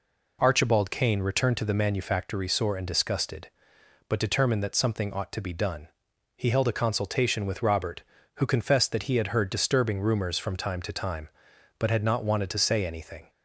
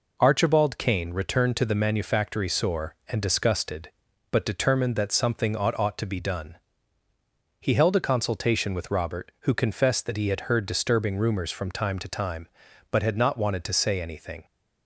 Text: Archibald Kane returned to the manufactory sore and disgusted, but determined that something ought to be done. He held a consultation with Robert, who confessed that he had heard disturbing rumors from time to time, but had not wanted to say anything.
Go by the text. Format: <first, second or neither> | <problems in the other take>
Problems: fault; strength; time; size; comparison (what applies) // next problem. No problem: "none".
first | says "ought" twice; at 5.7 s